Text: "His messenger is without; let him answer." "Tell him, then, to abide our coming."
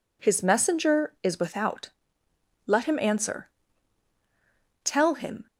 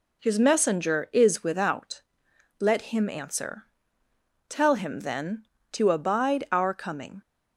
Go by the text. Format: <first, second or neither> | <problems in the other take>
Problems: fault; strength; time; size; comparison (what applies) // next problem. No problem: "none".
second | stops before "then to abide our coming"; at 5.4 s